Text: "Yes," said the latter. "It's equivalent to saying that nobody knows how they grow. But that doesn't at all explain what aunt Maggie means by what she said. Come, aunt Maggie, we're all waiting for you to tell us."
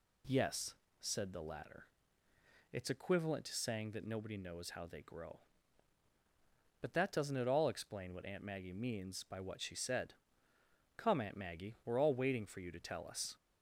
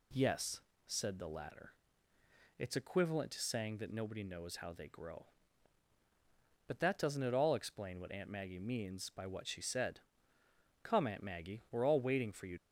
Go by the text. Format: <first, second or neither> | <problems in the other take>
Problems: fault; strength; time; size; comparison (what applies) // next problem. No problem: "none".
first | stops before "to tell us"; at 12.5 s